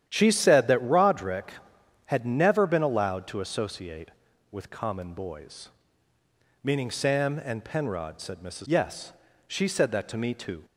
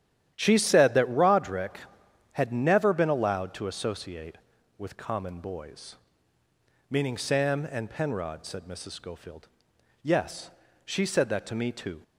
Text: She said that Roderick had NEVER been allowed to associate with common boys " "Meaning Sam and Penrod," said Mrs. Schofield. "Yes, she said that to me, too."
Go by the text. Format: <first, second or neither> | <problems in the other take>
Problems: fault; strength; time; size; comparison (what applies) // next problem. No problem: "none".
second | starts louder than the rest; strong; until 1.0 s; 10.5 dB; strong in the second // skips "Schofield"; at 8.6 s